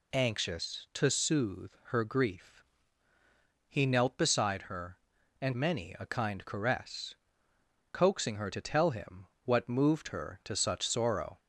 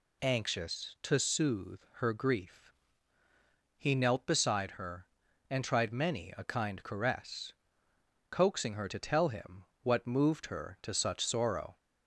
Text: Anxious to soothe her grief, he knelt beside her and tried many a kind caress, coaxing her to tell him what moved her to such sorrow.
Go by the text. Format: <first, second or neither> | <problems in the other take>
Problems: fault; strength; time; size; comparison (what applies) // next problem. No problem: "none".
second | skips "tried"; at 5.5 s // pauses between "him" and "what"; slight; at 9.2 s; 0.18 s long; slight in the second